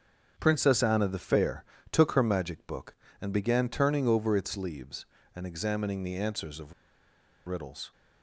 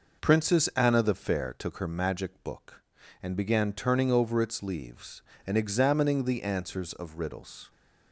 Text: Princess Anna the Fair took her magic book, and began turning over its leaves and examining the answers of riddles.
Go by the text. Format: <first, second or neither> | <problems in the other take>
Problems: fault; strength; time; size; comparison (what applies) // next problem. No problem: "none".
second | starts louder than the rest; strong; until 1.3 s; 7.5 dB // pauses between "Fair" and "took"; slight; at 1.6 s; 0.26 s long // pauses between "of" and "riddles"; noticeable; at 6.7 s; 0.74 s long